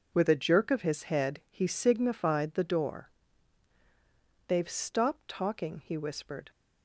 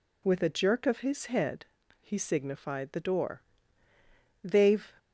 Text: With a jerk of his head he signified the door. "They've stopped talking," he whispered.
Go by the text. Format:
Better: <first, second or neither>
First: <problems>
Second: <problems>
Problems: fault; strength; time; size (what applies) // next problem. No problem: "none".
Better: first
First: none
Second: pauses between "head" and "he"; slight; at 1.6 s; 0.34 s long // stops before "stopped talking he whispered"; at 4.9 s